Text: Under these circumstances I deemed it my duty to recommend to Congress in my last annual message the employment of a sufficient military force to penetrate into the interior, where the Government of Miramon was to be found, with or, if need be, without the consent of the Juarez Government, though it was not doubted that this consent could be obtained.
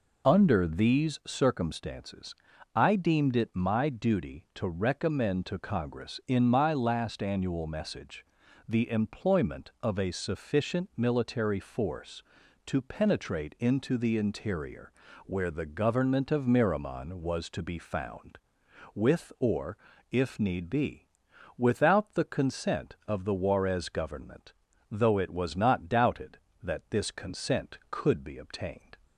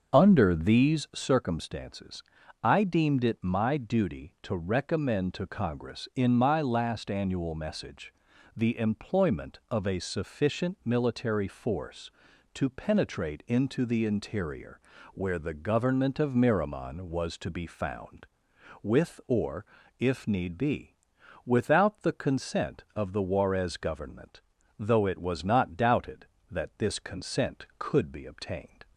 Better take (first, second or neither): first